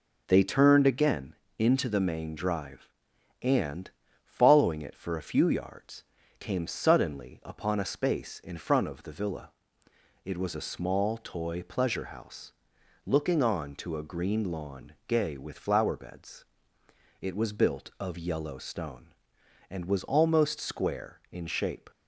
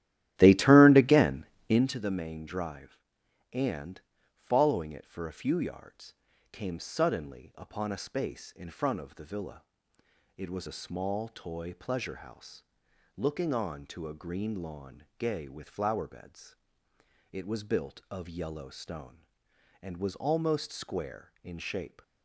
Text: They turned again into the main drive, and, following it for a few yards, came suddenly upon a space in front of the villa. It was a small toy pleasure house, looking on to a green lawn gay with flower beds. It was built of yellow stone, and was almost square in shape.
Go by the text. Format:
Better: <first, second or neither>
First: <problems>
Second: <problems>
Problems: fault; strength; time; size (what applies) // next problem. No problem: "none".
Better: first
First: pauses between "again" and "into"; slight; at 1.3 s; 0.24 s long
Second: starts louder than the rest; strong; until 1.9 s; 12.5 dB // pauses between "again" and "into"; slight; at 1.4 s; 0.24 s long